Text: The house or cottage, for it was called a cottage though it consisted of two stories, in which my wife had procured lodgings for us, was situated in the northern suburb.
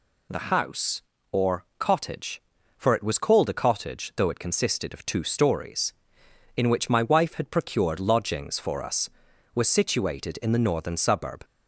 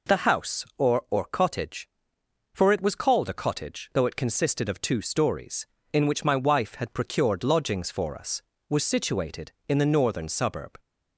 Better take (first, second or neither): first